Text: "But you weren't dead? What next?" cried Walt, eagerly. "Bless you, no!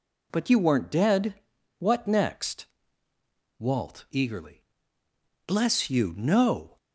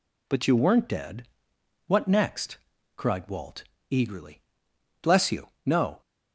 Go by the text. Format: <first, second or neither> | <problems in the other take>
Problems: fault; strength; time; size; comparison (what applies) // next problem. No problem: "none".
second | skips "cried"; at 3.1 s